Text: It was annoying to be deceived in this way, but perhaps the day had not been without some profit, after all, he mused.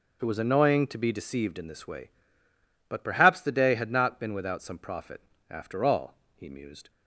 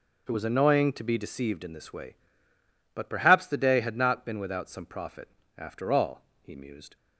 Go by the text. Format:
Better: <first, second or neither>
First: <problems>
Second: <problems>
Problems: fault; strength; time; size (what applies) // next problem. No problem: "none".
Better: neither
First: none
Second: none